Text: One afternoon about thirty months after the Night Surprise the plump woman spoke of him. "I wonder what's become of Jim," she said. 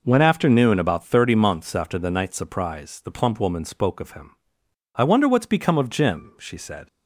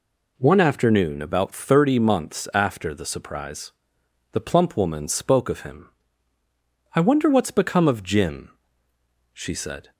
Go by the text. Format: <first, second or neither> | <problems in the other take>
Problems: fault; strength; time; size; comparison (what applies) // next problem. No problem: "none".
first | skips "Night"; at 3.0 s // pauses between "Surprise" and "the"; noticeable; at 3.7 s; 0.62 s long